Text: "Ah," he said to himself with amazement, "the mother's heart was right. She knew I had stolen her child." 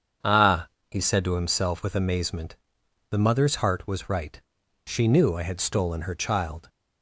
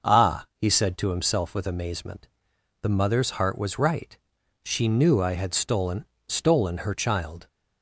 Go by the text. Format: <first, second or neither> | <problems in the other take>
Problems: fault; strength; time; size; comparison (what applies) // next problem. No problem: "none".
first | starts louder than the rest; noticeable; until 1.1 s; 6 dB; strong in the first // says "stolen" twice; at 6.2 s